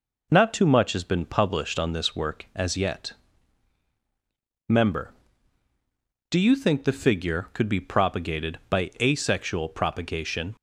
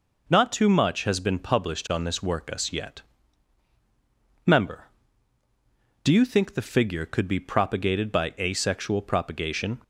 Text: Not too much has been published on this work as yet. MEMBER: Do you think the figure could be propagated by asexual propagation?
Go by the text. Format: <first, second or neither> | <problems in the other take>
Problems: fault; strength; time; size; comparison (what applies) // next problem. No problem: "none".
first | says "us" for "as"; at 2.5 s